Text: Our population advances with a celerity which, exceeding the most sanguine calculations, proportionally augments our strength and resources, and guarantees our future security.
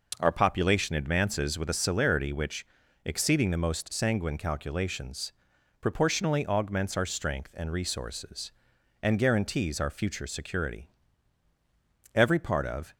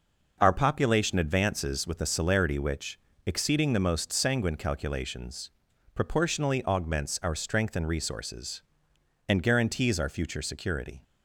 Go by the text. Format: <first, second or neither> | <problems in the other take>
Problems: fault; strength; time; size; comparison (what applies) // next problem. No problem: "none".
second | goes on to say "Every part of"; noticeable; from 12.1 s on; 0.78 s long